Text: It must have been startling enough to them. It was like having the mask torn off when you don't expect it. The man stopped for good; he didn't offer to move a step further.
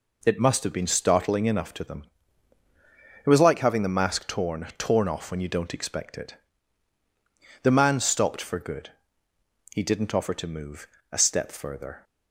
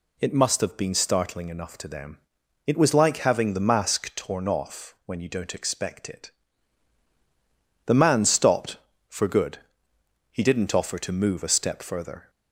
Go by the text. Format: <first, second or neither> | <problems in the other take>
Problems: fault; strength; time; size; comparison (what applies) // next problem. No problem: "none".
second | says "torn" twice; at 4.7 s // pauses between "move" and "a"; slight; at 10.8 s; 0.26 s long